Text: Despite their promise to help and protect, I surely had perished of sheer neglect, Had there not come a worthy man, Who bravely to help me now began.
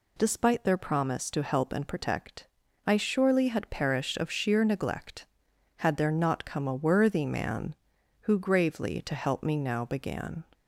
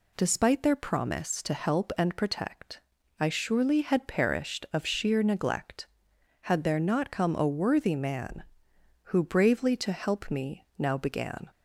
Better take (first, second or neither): second